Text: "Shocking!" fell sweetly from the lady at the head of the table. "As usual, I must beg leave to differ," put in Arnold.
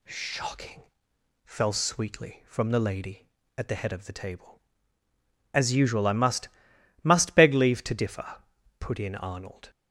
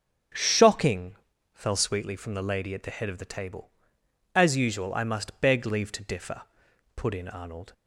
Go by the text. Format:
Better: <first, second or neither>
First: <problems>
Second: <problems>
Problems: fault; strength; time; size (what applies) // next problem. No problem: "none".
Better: second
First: says "must" twice; at 7.0 s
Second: none